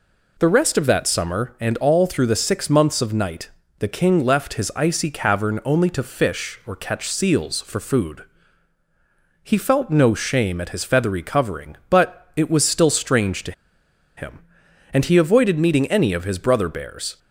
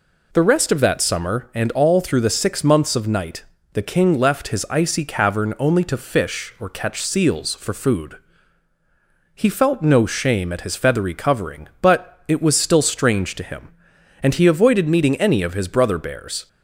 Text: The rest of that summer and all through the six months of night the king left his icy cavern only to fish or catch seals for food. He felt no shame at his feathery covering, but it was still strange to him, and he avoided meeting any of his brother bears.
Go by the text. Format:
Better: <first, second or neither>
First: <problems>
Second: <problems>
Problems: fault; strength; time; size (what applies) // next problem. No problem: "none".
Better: second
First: pauses between "night" and "the"; slight; at 3.4 s; 0.30 s long // pauses between "to" and "him"; noticeable; at 13.5 s; 0.65 s long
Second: pauses between "night" and "the"; slight; at 3.4 s; 0.30 s long